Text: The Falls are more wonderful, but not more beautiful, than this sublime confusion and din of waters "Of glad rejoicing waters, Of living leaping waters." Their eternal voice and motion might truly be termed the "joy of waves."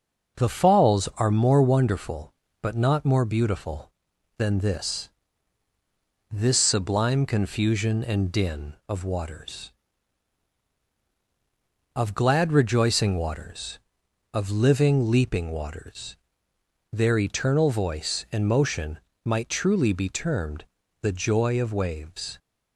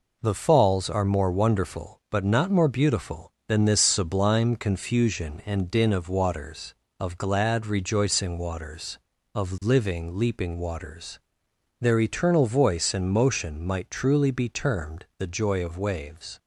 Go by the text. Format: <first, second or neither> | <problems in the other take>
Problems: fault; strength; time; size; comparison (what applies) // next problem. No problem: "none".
second | says "this" twice; at 6.3 s // pauses between "motion" and "might"; slight; at 18.9 s; 0.26 s long // pauses between "termed" and "the"; at 20.6 s; 0.38 s long